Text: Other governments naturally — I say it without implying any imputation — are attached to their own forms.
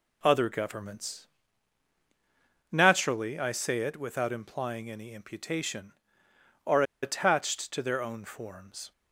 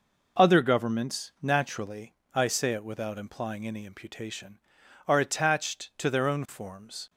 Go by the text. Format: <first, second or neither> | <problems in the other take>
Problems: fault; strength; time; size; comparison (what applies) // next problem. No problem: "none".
second | pauses between "governments" and "naturally"; strong; at 1.2 s; 1.4 s long // pauses between "are" and "attached"; slight; at 6.8 s; 0.19 s long